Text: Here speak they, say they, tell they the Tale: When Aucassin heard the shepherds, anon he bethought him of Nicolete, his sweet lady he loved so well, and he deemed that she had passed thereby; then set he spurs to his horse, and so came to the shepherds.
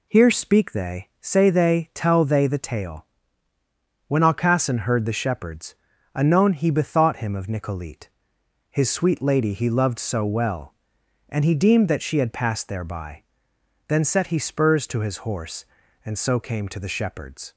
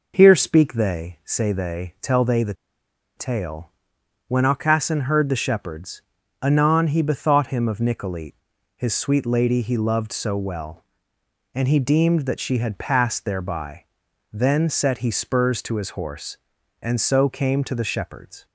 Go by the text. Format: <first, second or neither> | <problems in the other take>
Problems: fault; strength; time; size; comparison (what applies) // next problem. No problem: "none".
first | pauses between "the" and "Tale"; noticeable; at 2.5 s; 0.63 s long